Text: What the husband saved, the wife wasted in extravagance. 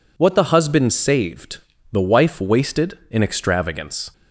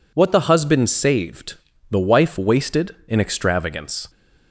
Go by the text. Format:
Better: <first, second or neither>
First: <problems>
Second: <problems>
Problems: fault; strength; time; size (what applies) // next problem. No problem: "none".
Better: neither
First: none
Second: none